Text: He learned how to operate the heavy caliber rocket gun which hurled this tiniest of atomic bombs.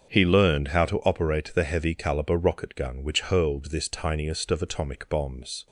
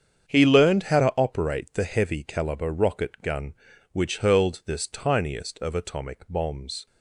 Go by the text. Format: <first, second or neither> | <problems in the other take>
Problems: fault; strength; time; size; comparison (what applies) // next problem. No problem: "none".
neither | starts louder than the rest; strong; the same in both